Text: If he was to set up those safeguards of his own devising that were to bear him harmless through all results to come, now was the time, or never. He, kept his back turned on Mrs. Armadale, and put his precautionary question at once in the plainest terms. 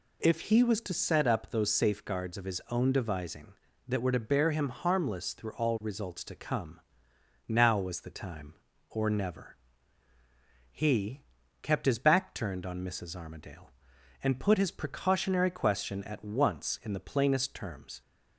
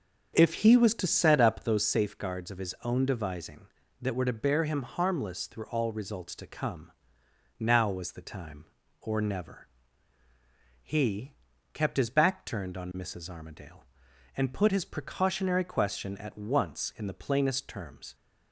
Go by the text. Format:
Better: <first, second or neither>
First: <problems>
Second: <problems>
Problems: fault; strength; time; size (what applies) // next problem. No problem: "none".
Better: first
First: none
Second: starts louder than the rest; until 1.9 s; 6.5 dB